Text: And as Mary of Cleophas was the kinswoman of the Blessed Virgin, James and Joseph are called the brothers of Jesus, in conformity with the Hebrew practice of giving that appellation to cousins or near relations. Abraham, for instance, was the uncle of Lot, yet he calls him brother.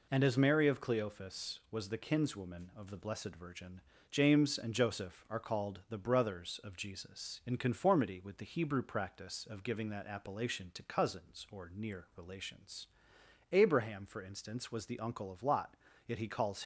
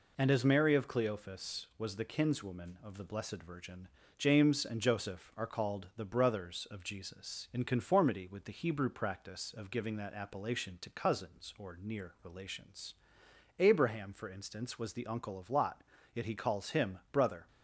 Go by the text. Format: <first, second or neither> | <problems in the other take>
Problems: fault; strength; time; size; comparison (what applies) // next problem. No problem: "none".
second | stops before "him brother"; at 16.6 s